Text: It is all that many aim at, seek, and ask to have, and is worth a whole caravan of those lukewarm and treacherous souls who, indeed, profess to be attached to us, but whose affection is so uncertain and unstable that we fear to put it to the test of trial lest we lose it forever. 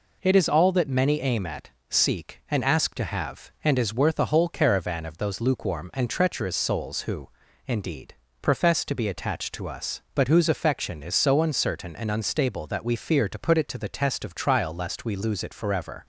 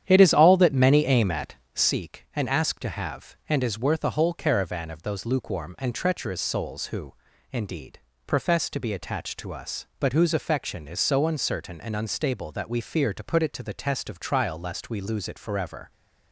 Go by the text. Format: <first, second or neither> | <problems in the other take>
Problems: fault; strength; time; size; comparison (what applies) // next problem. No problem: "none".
first | starts louder than the rest; strong; until 1.9 s; 9.5 dB